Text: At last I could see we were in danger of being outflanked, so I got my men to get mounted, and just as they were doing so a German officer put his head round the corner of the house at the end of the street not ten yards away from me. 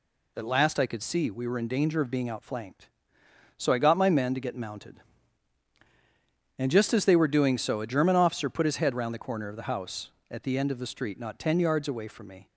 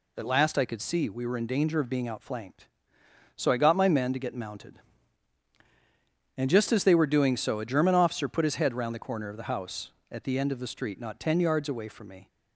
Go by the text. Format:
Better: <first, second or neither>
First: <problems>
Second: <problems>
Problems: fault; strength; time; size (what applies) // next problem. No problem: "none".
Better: neither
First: none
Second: none